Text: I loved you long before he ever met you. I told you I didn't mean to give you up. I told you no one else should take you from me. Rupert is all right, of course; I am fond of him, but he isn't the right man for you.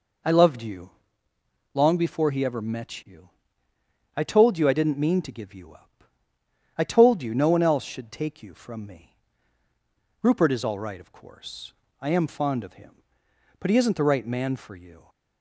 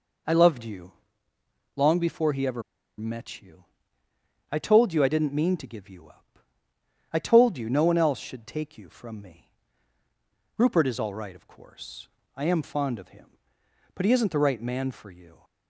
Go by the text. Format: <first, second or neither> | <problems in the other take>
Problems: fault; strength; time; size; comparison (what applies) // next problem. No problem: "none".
first | pauses between "you" and "long"; noticeable; at 0.9 s; 0.84 s long; noticeable in the first // pauses between "ever" and "met"; slight; at 2.6 s; 0.35 s long